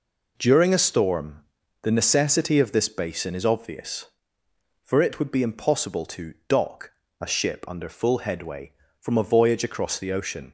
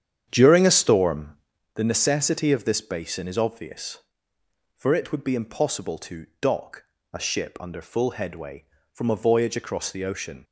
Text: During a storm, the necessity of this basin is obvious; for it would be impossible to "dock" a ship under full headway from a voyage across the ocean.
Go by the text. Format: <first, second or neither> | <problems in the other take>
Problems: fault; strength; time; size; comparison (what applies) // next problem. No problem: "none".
first | starts louder than the rest; strong; until 1.6 s; 8.5 dB // pauses between "to" and "dock"; slight; at 6.2 s; 0.16 s long; slight in the first // pauses between "dock" and "a"; slight; at 6.8 s; 0.30 s long; slight in the first